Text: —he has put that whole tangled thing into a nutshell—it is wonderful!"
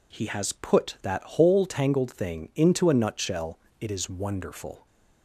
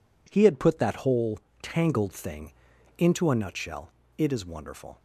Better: first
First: none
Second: says "had" for "has"; at 0.4 s // pauses between "whole" and "tangled"; slight; at 1.3 s; 0.22 s long // pauses between "thing" and "into"; noticeable; at 2.5 s; 0.46 s long

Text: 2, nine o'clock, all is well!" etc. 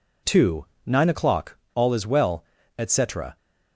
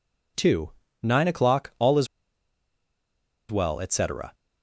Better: first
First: none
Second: pauses between "is" and "well"; strong; at 2.0 s; 1.4 s long

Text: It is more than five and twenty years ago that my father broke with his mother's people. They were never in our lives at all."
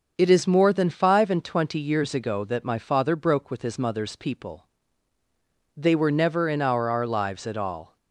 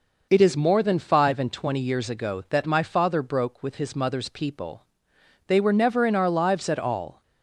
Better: second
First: starts louder than the rest; until 1.1 s; 6.5 dB // says "our" twice; at 6.9 s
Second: none

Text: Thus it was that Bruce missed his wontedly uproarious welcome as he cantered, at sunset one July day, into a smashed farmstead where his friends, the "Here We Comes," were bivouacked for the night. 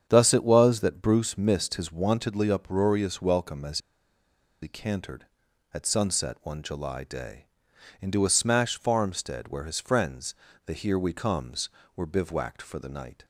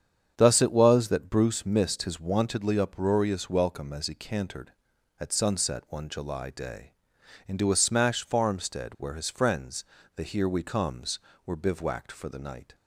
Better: second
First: starts louder than the rest; strong; until 1.1 s; 7.5 dB // pauses between "as" and "he"; noticeable; at 3.7 s; 0.83 s long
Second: starts louder than the rest; strong; until 1.3 s; 7.5 dB

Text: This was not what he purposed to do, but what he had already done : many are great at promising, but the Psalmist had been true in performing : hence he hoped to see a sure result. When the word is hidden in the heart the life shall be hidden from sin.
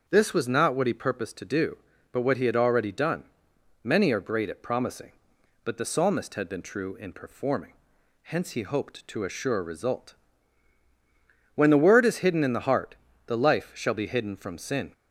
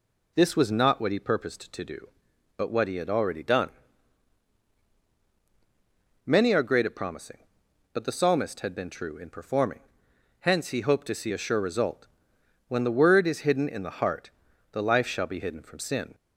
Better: second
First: starts louder than the rest; until 1.0 s; 7 dB // skips "see"; at 9.2 s // pauses between "heart" and "the"; slight; at 12.9 s; 0.32 s long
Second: pauses between "heart" and "the"; at 14.2 s; 0.42 s long

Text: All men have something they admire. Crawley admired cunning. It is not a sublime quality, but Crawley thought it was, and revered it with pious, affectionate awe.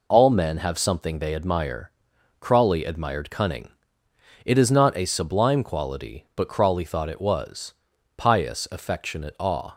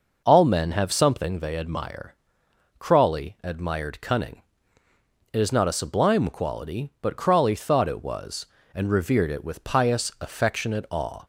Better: second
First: skips "and revered it with"; at 7.9 s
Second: none

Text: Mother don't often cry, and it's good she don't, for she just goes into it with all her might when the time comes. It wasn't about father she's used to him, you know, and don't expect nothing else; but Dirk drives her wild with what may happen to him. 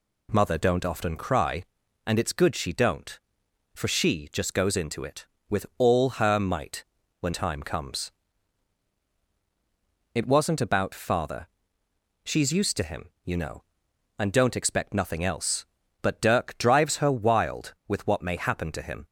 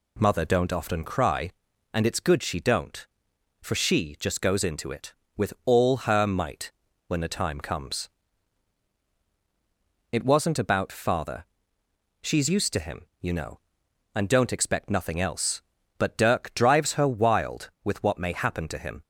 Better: second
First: pauses between "might" and "when"; slight; at 6.8 s; 0.36 s long // skips "the"; at 7.3 s // pauses between "father" and "she's"; noticeable; at 11.4 s; 0.76 s long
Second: pauses between "might" and "when"; slight; at 6.7 s; 0.36 s long // pauses between "father" and "she's"; noticeable; at 11.4 s; 0.76 s long

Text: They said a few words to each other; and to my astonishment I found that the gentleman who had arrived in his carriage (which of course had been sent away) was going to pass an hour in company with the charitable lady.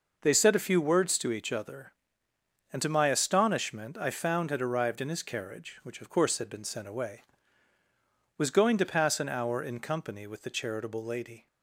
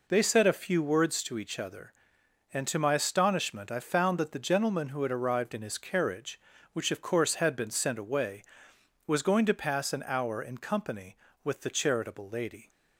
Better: second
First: skips "that the gentleman who"; at 4.5 s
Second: none

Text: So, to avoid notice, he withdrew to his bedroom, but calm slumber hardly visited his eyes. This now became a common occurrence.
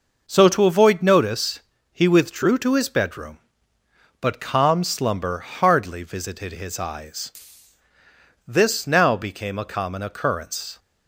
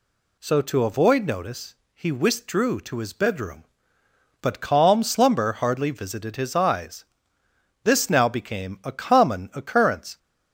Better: neither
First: none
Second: none

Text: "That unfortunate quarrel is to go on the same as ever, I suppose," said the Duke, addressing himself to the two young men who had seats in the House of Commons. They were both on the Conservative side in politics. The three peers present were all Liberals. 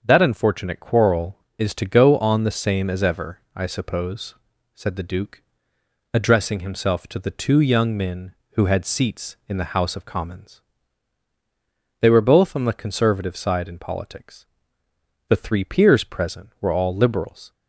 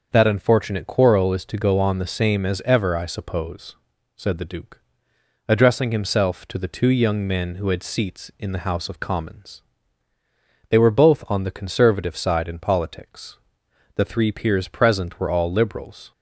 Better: neither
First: starts louder than the rest; until 1.0 s; 6.5 dB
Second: starts louder than the rest; until 1.1 s; 6.5 dB

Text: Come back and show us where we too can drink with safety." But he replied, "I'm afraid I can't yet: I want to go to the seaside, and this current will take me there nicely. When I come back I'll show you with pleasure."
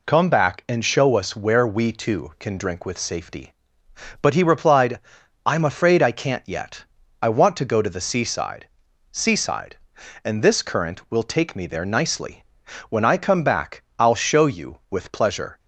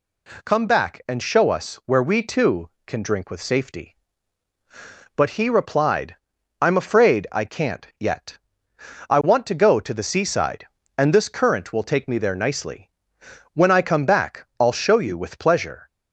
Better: second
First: says "seaside" twice; at 9.1 s // pauses between "back" and "I'll"; slight; at 13.8 s; 0.16 s long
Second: none

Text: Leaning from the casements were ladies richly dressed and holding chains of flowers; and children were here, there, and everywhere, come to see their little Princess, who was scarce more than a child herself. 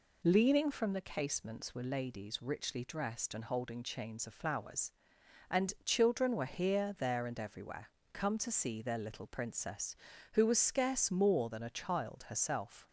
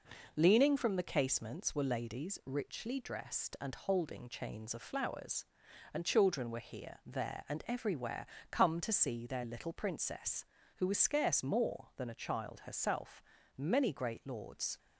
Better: first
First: none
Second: goes on to say "Many great lords"; noticeable; from 13.5 s on; 1.2 s long

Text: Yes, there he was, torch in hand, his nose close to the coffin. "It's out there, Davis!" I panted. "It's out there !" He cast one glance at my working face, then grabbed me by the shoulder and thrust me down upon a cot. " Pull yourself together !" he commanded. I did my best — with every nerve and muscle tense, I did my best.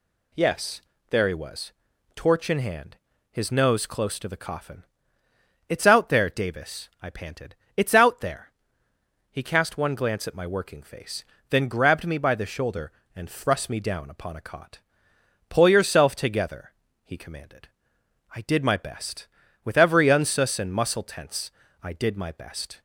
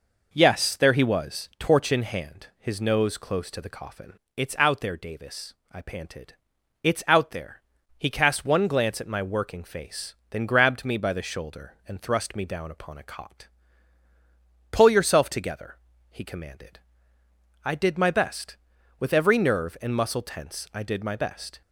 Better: second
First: says "unsus" for "nerve"; at 20.0 s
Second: none

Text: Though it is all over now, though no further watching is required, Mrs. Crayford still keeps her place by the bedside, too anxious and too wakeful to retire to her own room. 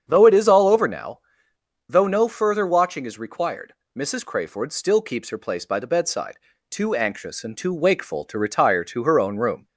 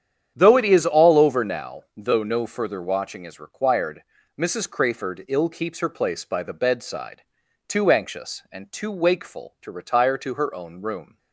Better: first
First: starts louder than the rest; strong; until 1.0 s; 7.5 dB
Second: starts louder than the rest; strong; until 1.3 s; 9 dB // says "ill" for "still"; at 5.2 s

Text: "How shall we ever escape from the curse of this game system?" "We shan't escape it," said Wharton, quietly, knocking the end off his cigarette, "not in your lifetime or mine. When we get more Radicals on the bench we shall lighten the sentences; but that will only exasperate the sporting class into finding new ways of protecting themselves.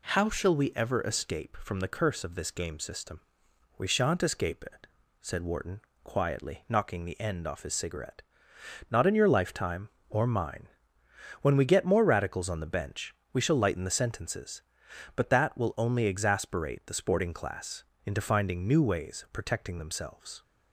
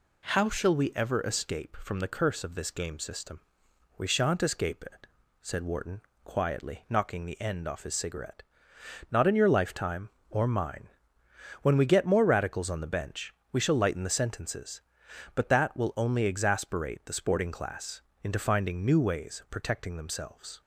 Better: neither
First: pauses between "bench" and "we"; slight; at 13.1 s; 0.16 s long // pauses between "class" and "into"; slight; at 17.8 s; 0.22 s long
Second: pauses between "bench" and "we"; slight; at 13.3 s; 0.16 s long // pauses between "class" and "into"; slight; at 18.0 s; 0.22 s long

